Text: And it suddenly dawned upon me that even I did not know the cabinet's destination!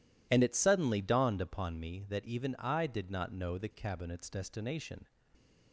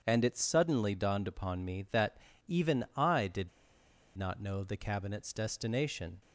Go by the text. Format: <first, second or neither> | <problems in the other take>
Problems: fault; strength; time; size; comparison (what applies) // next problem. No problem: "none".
first | pauses between "that" and "even"; slight; at 2.1 s; 0.30 s long // pauses between "did" and "not"; noticeable; at 3.4 s; 0.69 s long